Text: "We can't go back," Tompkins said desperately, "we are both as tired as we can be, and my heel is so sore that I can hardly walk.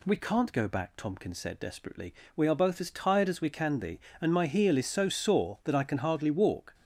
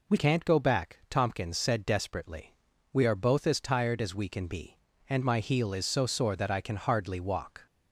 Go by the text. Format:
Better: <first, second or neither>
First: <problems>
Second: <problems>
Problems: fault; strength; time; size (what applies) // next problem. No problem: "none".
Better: first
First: none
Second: changes voice at "can't"; from 0.1 s on; 7.5 s long